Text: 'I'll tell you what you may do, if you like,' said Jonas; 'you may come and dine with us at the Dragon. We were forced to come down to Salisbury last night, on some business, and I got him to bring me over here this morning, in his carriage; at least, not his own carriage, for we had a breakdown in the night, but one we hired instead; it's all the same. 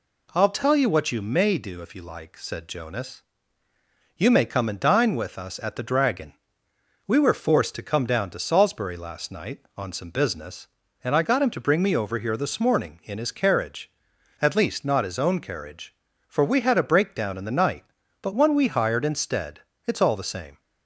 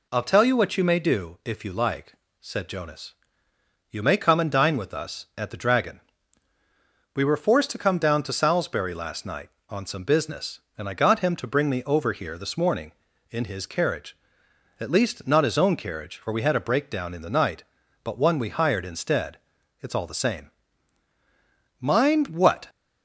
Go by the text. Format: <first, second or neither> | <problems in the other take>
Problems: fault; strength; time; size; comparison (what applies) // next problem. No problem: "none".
first | goes on to say "Mind what"; noticeable; from 21.8 s on; 0.86 s long